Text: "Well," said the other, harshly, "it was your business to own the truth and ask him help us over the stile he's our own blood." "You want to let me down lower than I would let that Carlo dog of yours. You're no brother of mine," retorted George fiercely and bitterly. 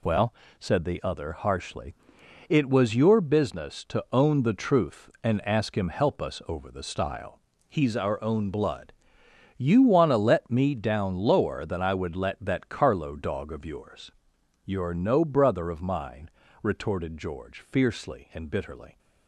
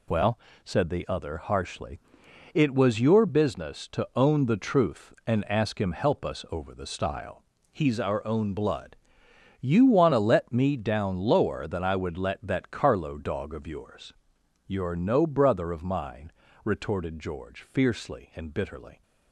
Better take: neither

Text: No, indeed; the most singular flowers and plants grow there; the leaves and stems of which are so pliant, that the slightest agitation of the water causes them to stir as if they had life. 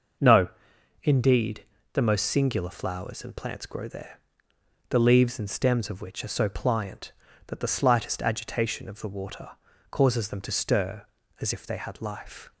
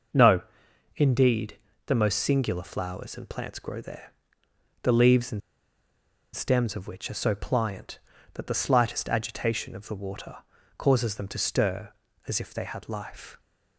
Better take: first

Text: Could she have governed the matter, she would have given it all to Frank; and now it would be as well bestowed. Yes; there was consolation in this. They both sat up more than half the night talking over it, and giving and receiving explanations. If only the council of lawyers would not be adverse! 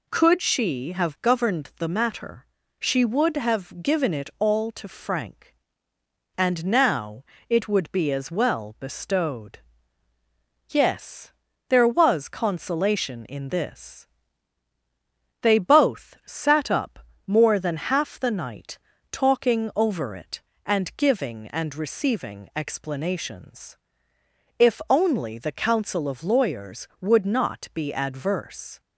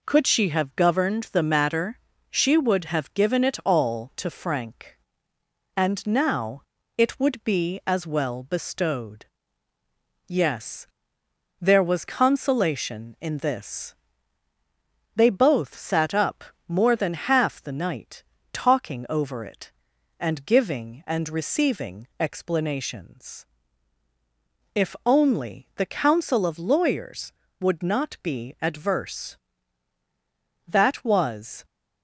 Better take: first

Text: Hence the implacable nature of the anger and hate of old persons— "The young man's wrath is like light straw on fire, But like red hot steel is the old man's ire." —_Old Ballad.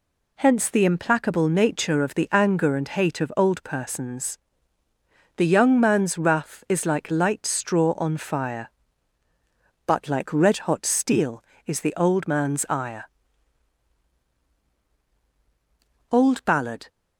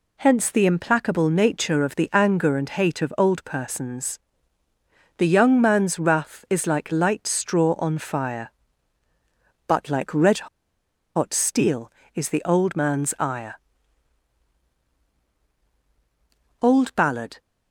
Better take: first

